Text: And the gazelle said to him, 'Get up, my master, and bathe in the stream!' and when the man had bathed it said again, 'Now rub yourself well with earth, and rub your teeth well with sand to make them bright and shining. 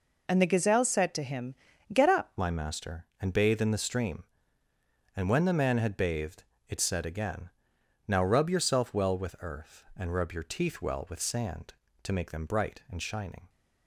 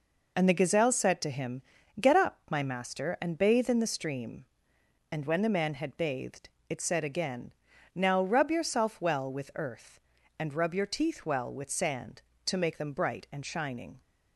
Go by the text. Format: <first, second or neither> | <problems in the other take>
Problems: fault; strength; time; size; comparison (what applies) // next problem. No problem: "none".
second | changes voice at "my"; from 2.3 s on; 11.1 s long // pauses between "bathed" and "it"; slight; at 6.4 s; 0.26 s long; slight in the second